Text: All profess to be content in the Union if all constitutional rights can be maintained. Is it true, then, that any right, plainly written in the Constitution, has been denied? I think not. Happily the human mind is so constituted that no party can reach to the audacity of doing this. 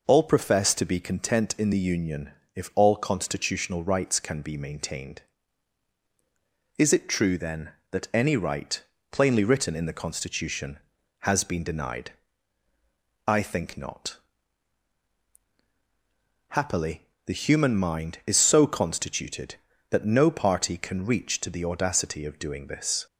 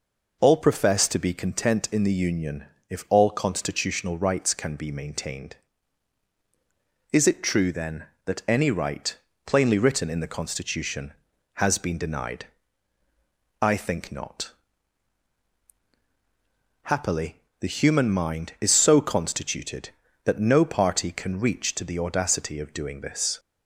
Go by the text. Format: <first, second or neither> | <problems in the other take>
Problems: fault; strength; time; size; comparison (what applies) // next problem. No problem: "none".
neither | pauses between "Union" and "if"; slight; the same in both // pauses between "Happily" and "the"; slight; the same in both